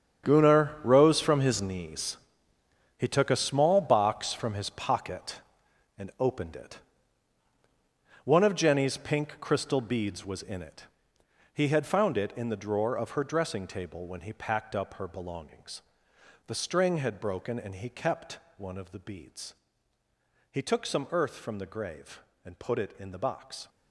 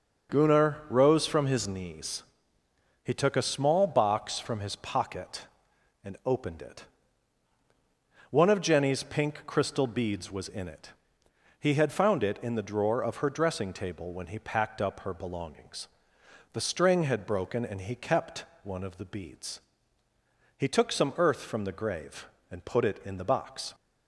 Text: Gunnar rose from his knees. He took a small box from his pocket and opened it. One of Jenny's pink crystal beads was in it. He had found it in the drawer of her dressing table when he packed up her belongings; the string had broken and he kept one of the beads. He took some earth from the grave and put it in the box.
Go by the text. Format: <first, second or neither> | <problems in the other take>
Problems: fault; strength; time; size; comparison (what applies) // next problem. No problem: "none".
second | gets quieter; strong; throughout; 13.5 dB // starts louder than the rest; strong; until 1.3 s; 8.5 dB; also in the second // pauses between "kept" and "one"; slight; at 18.3 s; 0.18 s long; slight in the second